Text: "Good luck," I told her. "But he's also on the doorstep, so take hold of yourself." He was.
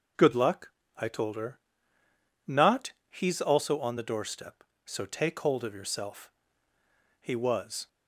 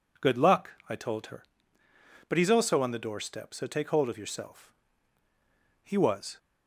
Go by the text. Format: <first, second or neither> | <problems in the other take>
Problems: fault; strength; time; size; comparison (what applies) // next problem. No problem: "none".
second | starts louder than the rest; noticeable; until 1.4 s; 6 dB // says "Not" for "But"; at 2.4 s